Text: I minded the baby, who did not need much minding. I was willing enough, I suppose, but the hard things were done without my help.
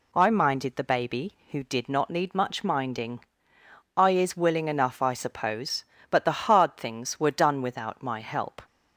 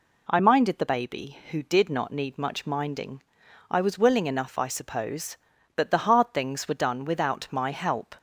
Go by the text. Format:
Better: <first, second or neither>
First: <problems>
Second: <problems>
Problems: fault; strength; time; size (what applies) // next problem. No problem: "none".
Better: second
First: says "is" for "was"; at 4.1 s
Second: none